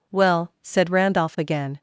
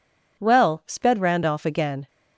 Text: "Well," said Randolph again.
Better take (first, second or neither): first